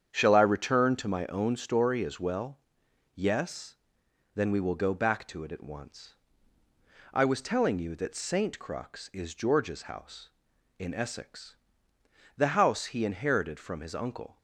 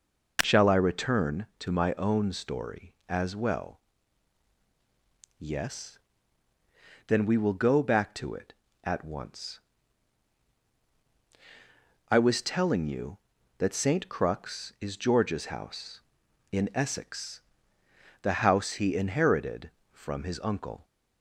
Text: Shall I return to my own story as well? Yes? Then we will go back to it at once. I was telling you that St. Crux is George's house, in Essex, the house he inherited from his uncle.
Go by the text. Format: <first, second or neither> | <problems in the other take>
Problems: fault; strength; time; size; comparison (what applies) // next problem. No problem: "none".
second | starts louder than the rest; strong; until 1.2 s; 8 dB